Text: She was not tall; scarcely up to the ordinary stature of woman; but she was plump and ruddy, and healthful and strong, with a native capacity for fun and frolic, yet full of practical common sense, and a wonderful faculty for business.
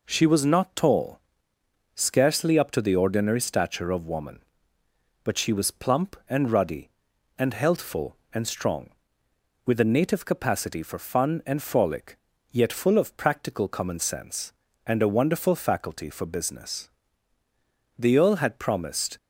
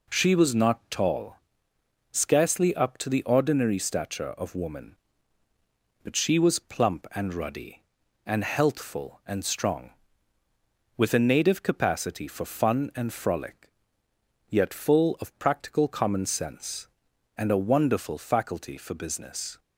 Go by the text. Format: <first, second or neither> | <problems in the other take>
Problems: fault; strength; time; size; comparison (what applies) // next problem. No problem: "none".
second | goes on to say "The earl had promised"; noticeable; from 17.9 s on; 1.1 s long